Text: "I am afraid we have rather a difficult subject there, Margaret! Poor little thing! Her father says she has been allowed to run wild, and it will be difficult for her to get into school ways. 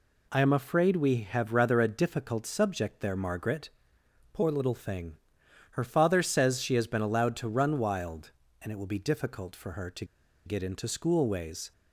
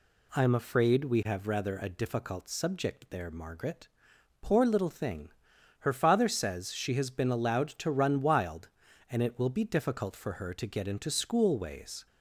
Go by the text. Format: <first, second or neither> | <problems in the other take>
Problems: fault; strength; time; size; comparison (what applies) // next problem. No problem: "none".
second | pauses between "to" and "get"; at 10.0 s; 0.41 s long